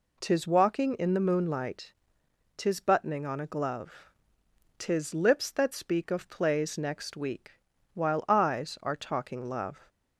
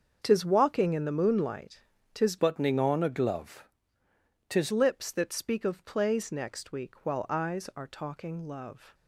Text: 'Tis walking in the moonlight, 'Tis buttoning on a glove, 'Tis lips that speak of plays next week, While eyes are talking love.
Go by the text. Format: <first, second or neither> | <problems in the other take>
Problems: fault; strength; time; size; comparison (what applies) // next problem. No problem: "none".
first | starts louder than the rest; until 1.2 s; 6.5 dB // changes voice from "buttoning" to "Tis"; from 2.3 to 4.7 s; 2.4 s long